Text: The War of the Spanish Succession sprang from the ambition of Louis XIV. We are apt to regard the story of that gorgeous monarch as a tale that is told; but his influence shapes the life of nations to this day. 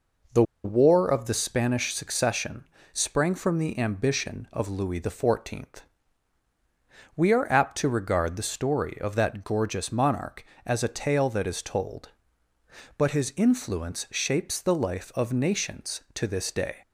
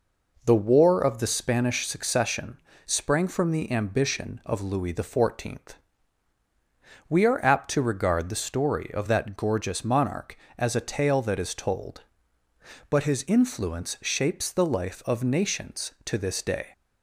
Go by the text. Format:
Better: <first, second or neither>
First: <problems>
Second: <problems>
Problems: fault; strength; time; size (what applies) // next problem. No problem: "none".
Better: second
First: pauses between "The" and "War"; slight; at 0.4 s; 0.21 s long // pauses between "Succession" and "sprang"; slight; at 2.6 s; 0.24 s long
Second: pauses between "Succession" and "sprang"; slight; at 2.6 s; 0.24 s long